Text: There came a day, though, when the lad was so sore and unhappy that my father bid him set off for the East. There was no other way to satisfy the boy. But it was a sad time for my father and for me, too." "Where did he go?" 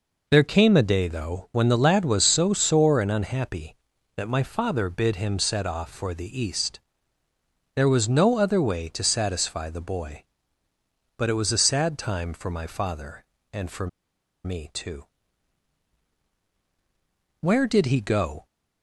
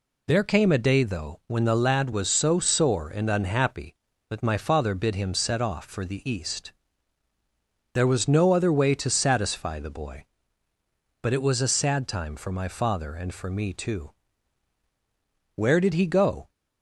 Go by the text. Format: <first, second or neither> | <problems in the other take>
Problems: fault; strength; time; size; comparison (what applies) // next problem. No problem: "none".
second | pauses between "for" and "me"; noticeable; at 13.8 s; 0.57 s long